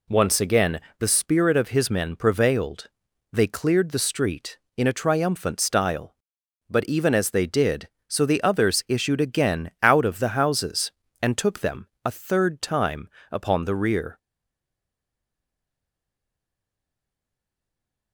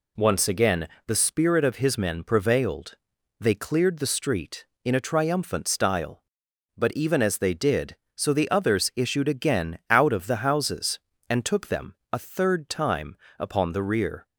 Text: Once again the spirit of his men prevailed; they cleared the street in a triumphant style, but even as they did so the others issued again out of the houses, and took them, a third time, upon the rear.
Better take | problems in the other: second | pauses between "again" and "the"; slight; at 0.7 s; 0.20 s long; slight in the second // stays silent after the last word; strong; from 14.1 s on; 4.0 s long

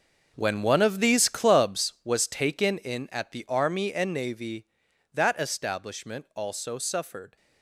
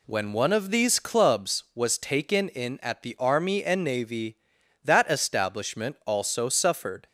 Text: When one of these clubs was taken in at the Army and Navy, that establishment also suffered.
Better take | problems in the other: second | gets quieter; strong; throughout; 12.5 dB

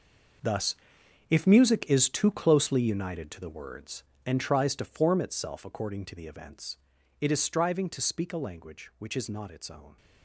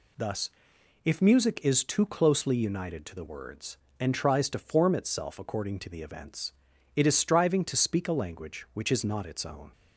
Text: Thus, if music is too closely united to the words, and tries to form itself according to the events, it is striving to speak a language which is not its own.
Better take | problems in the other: second | gets quieter; strong; throughout; 13 dB

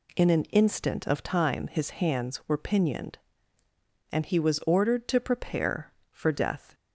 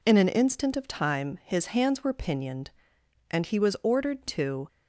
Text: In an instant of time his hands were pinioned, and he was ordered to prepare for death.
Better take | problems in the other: first | stops before "prepare for death"; at 4.6 s

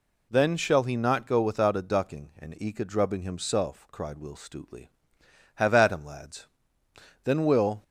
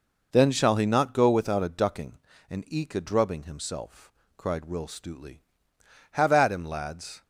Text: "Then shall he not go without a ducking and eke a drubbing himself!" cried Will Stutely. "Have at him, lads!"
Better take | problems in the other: second | goes on to say "Then Will"; from 7.2 s on; 0.58 s long

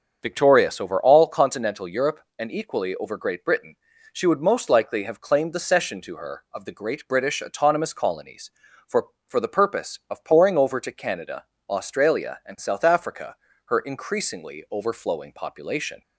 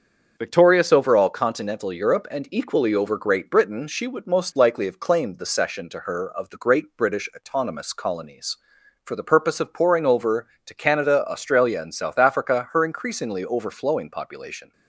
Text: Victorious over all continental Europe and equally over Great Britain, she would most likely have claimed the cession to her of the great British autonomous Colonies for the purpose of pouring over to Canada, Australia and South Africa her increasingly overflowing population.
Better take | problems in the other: second | starts louder than the rest; until 1.2 s; 7 dB; also in the second // says "for" twice; at 9.2 s // pauses between "Africa" and "her"; slight; at 13.3 s; 0.28 s long

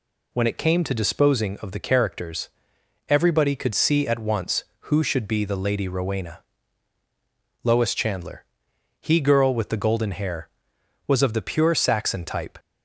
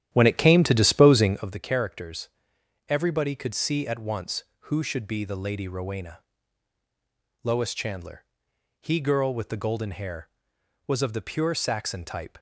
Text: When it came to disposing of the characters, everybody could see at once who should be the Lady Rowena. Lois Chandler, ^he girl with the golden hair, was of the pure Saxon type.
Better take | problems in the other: first | starts louder than the rest; strong; until 1.6 s; 11.5 dB

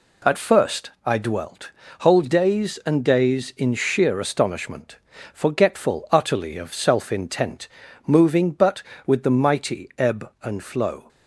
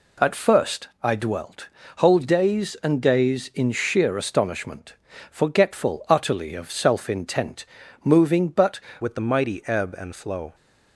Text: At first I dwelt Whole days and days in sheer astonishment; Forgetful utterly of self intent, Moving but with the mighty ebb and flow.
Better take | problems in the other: first | pauses between "dwelt" and "Whole"; slight; at 1.6 s; 0.28 s long; slight in the first // changes voice at "with"; from 9.0 s on; 1.5 s long

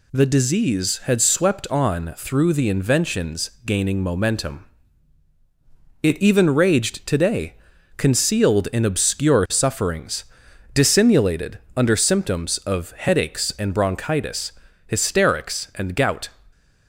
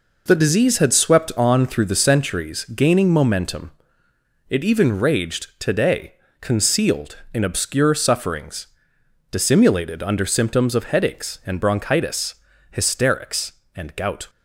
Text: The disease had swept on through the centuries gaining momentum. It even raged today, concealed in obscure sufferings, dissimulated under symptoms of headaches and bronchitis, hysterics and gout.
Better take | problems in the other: second | says "inventions" for "centuries"; at 2.6 s // pauses between "dissimulated" and "under"; slight; at 11.5 s; 0.16 s long

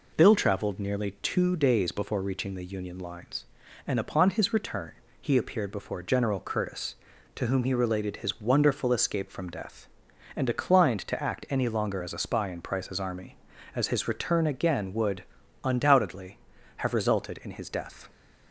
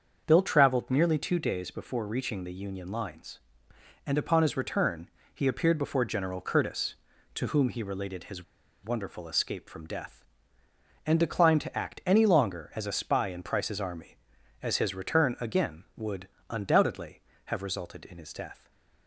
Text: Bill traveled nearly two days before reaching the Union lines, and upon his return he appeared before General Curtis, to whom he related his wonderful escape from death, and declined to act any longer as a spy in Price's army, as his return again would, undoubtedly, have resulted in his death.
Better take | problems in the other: first | starts louder than the rest; until 1.2 s; 7 dB // pauses between "return" and "he"; slight; at 5.0 s; 0.26 s long; slight in the first // pauses between "his" and "wonderful"; at 8.4 s; 0.39 s long // stays silent after the last word; slight; from 18.5 s on; 0.5 s long

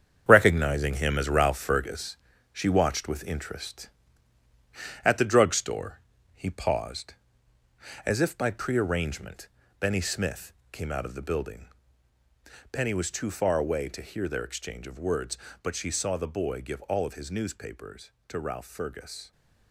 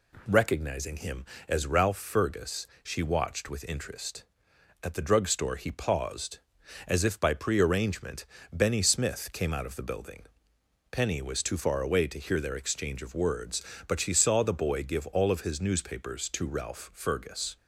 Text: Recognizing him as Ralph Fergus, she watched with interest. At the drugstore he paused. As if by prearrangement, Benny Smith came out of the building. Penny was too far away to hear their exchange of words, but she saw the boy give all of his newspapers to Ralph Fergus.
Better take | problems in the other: second | gets quieter; strong; throughout; 8.5 dB // pauses between "drugstore" and "he"; slight; at 6.0 s; 0.34 s long // pauses between "Smith" and "came"; slight; at 10.5 s; 0.20 s long

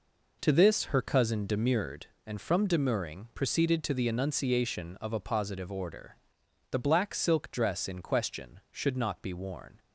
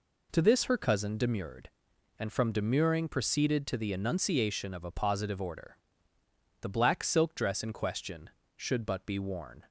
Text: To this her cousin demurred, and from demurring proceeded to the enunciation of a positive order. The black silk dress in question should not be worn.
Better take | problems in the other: first | says "but" for "not"; at 8.8 s

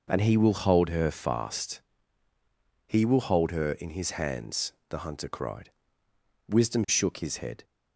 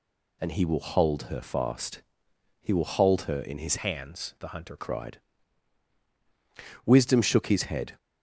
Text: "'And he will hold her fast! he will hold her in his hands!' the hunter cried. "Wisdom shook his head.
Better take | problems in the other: first | changes voice from "hands" to "hunter"; from 3.7 to 4.7 s; 1.0 s long

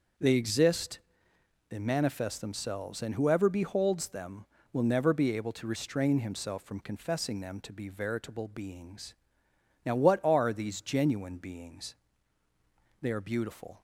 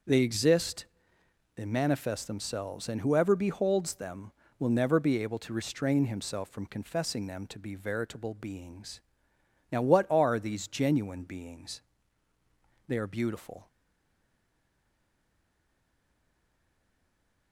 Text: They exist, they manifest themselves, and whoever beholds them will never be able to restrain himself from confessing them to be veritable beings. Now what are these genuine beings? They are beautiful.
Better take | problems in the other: first | starts louder than the rest; noticeable; until 1.7 s; 6 dB; noticeable in the first // stays silent after the last word; strong; from 13.6 s on; 3.9 s long

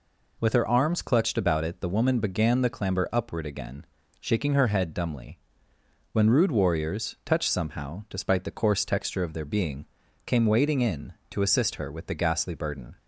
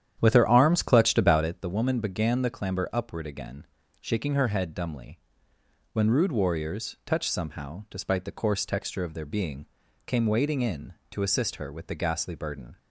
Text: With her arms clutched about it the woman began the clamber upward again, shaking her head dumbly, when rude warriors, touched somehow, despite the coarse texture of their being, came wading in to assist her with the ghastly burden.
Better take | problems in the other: first | starts louder than the rest; strong; until 1.6 s; 10 dB

